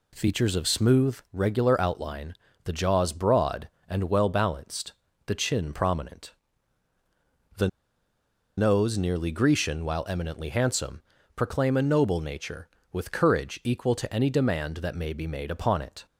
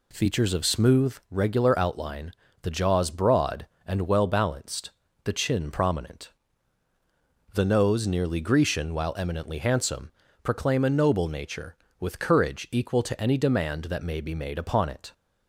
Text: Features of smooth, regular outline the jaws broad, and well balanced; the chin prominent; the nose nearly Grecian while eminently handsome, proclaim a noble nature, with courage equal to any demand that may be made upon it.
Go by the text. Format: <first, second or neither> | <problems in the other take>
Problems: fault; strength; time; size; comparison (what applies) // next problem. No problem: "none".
second | pauses between "outline" and "the"; slight; at 2.3 s; 0.32 s long; slight in the second // pauses between "the" and "nose"; noticeable; at 7.6 s; 0.89 s long